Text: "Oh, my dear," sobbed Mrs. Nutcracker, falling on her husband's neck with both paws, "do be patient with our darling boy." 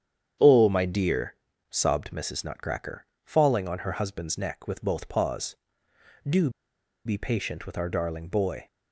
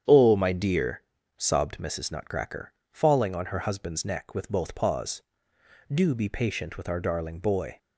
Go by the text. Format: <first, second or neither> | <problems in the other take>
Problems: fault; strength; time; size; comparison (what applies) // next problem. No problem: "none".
second | starts louder than the rest; strong; until 1.7 s; 8.5 dB; strong in the second // pauses between "do" and "be"; noticeable; at 6.4 s; 0.56 s long